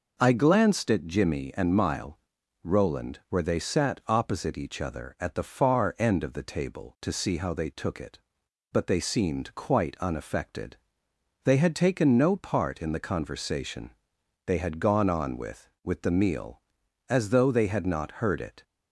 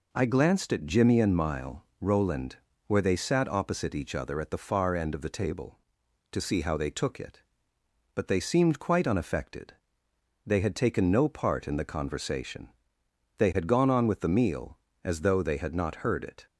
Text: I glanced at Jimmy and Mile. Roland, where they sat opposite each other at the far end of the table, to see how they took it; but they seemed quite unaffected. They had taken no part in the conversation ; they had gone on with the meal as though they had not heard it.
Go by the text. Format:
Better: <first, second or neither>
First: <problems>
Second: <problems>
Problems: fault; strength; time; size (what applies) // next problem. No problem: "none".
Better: second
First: says "with" twice; at 15.8 s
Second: none